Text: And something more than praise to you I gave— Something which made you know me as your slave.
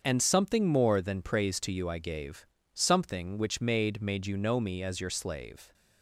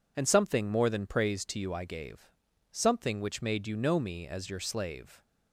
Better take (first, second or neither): second